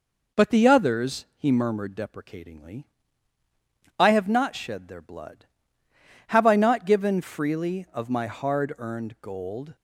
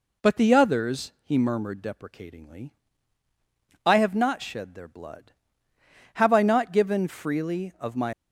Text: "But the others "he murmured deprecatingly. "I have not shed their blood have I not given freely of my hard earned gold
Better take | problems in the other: first | stops before "hard earned gold"; at 8.1 s

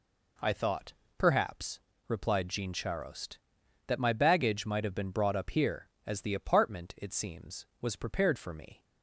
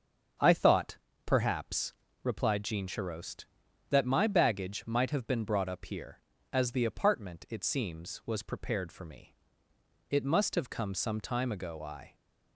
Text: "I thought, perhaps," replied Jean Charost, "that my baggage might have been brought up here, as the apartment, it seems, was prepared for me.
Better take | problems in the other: first | starts louder than the rest; until 1.6 s; 7 dB // goes on to say "It must have come some time ago I"; strong; from 10.1 s on; 2.0 s long

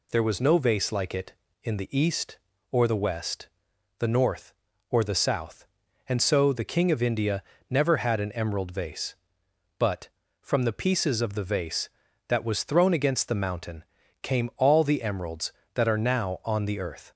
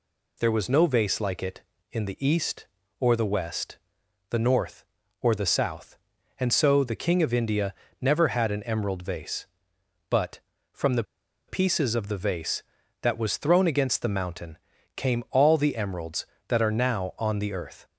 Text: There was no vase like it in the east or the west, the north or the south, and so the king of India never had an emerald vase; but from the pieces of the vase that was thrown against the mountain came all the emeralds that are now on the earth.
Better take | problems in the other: first | pauses between "India" and "never"; slight; at 7.7 s; 0.26 s long; slight in the first // pauses between "the" and "pieces"; at 11.0 s; 0.45 s long // pauses between "mountain" and "came"; at 14.5 s; 0.38 s long; also in the first

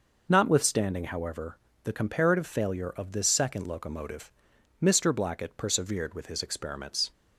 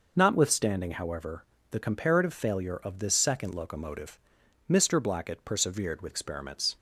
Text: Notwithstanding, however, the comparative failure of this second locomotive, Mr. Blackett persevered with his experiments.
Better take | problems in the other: first | skips "his"; at 6.1 s

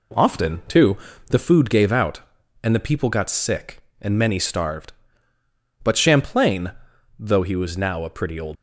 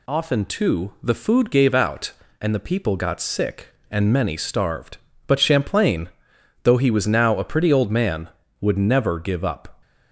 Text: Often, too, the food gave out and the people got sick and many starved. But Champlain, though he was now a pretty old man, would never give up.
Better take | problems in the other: second | stops before "man would never give up"; at 8.5 s

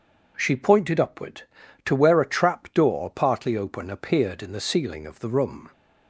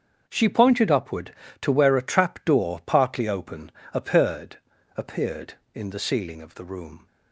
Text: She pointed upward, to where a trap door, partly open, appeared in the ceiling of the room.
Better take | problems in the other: first | starts louder than the rest; until 1.2 s; 7 dB // says "appeared" twice; at 4.9 s

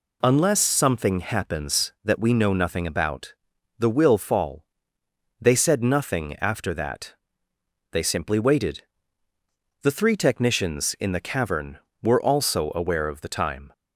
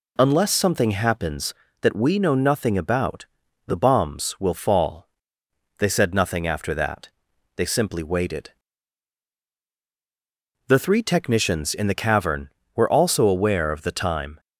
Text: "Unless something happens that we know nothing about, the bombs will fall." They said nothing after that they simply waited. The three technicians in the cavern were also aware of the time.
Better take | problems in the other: second | skips "bombs"; at 3.8 s // pauses between "that" and "they"; noticeable; at 7.1 s; 0.78 s long; noticeable in the second

